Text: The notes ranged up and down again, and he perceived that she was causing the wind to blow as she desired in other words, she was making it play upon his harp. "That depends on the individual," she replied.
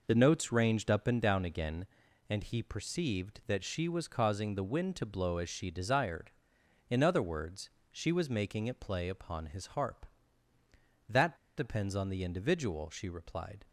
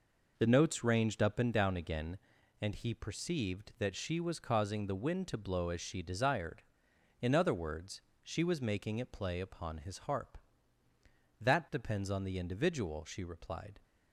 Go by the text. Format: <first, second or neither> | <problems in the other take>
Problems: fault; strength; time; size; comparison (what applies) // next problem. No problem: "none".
second | pauses between "That" and "depends"; slight; at 11.3 s; 0.19 s long